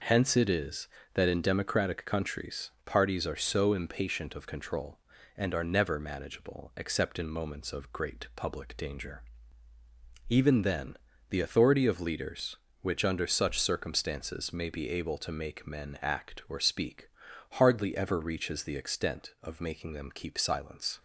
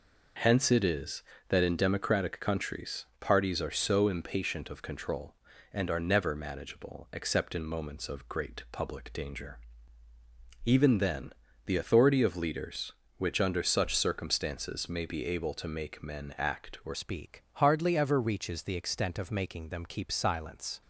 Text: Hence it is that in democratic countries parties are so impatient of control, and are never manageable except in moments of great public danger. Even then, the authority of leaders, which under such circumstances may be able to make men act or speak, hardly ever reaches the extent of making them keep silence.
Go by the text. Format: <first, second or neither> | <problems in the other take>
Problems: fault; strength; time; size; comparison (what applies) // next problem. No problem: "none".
first | changes voice at "speak"; from 16.9 s on; 3.9 s long